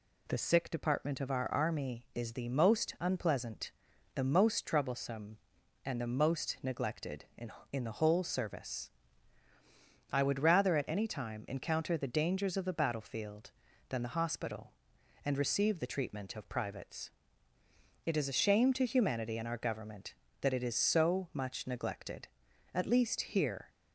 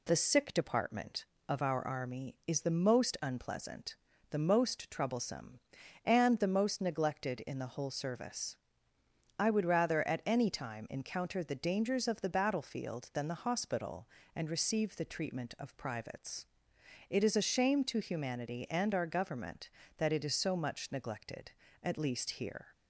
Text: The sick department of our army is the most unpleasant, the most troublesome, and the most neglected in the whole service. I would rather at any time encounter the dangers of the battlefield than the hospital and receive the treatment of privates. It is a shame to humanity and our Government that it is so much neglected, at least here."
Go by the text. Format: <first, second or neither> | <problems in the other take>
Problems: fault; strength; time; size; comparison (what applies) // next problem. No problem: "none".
second | says "in" twice; at 7.7 s